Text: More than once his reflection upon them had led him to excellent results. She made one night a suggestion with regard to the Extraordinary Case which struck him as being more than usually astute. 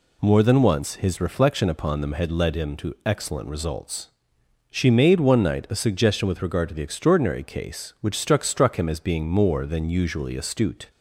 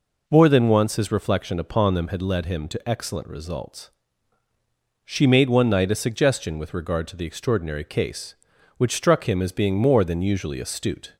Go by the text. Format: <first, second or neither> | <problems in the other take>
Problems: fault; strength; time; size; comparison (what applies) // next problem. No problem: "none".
second | says "struck" twice; at 8.4 s